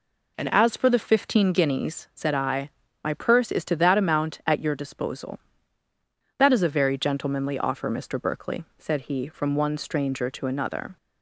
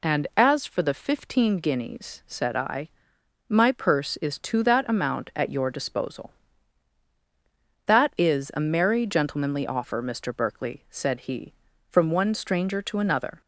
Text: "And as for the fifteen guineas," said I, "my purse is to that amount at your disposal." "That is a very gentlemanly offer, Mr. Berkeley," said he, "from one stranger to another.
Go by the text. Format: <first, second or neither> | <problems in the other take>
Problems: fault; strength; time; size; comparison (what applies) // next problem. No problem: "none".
first | says "merry" for "very"; at 8.6 s